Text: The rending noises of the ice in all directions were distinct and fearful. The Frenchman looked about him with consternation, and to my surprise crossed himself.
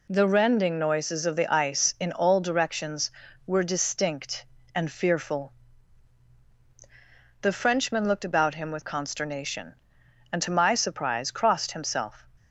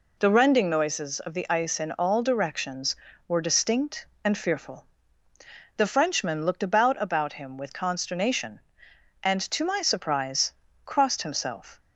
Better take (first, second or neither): first